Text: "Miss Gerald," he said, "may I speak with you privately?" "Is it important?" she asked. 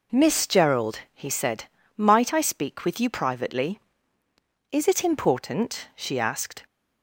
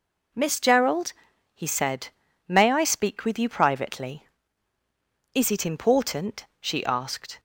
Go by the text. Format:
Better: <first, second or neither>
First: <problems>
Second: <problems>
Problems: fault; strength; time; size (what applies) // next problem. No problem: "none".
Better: second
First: says "might" for "may"; at 1.9 s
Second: none